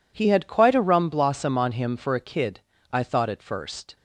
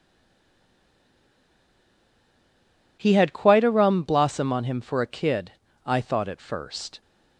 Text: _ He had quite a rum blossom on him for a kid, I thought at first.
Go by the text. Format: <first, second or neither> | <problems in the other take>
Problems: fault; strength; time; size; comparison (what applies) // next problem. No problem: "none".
first | stays silent before the first word; strong; until 2.9 s; 2.9 s long